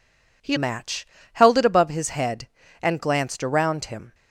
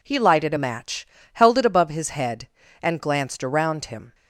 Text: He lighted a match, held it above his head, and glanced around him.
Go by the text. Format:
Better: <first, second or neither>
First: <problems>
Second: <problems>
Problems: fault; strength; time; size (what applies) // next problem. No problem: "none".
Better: second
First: skips "lighted a"; at 0.5 s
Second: none